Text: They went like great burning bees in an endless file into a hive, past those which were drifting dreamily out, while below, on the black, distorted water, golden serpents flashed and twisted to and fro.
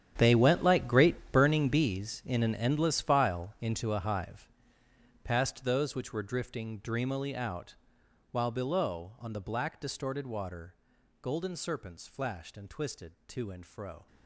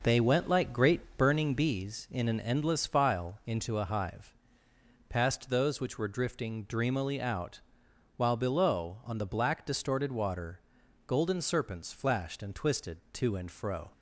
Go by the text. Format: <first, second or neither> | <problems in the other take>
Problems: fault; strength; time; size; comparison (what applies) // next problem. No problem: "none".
second | gets quieter; strong; throughout; 14.5 dB